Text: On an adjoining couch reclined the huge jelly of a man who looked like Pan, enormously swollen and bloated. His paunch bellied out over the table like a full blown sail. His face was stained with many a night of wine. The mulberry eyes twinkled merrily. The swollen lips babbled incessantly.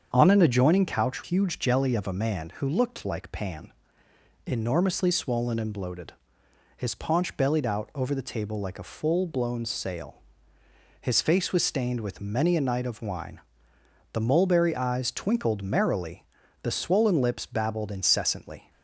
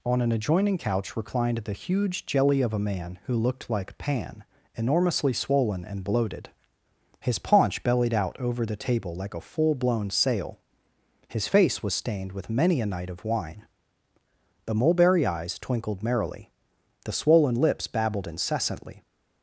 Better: second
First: starts louder than the rest; strong; until 1.1 s; 7.5 dB // skips "reclined the"; at 1.2 s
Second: none

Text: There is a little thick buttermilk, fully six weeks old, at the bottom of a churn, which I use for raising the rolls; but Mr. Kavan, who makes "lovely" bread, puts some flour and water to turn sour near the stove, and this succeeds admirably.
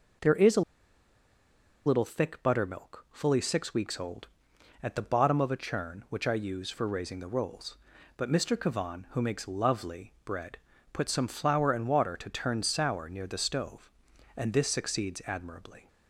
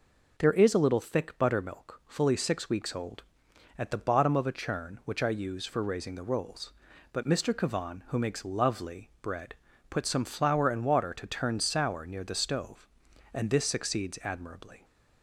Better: second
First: pauses between "a" and "little"; strong; at 0.6 s; 1.2 s long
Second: none

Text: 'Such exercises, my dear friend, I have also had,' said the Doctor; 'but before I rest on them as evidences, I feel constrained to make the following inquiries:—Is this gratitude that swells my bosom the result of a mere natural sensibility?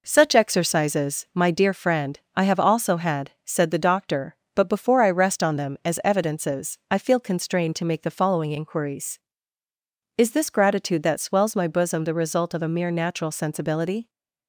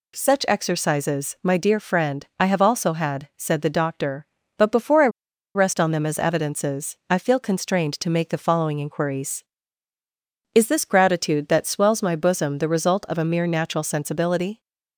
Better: first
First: none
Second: pauses between "I" and "rest"; noticeable; at 5.0 s; 0.46 s long

